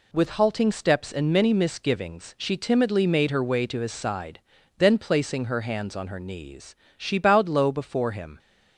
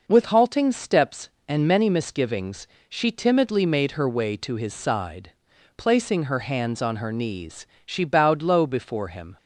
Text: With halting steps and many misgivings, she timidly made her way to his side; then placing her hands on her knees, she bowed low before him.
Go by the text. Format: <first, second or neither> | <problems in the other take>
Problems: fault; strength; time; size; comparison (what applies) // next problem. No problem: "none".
first | skips "then"; at 5.5 s